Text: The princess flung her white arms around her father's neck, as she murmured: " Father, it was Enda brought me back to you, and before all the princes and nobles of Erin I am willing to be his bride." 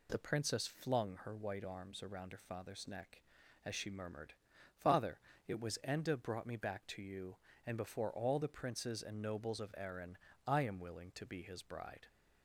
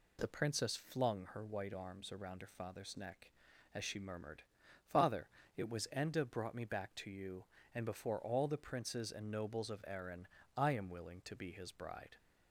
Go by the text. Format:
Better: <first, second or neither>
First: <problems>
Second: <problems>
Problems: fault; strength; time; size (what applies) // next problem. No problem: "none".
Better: neither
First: pauses between "Erin" and "I"; slight; at 10.1 s; 0.30 s long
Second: pauses between "Erin" and "I"; slight; at 10.2 s; 0.30 s long